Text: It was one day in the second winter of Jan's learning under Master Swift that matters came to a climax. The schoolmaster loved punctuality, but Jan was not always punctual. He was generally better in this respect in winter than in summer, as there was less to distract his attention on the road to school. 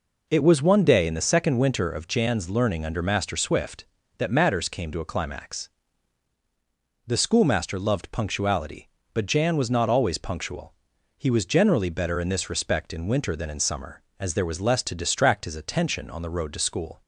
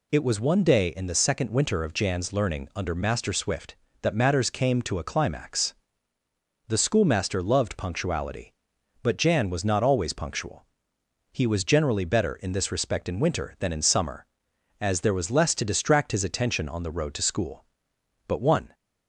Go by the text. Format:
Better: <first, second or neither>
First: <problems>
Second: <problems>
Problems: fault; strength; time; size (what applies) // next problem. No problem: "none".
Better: first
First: none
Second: goes on to say "But one"; slight; from 18.2 s on; 0.46 s long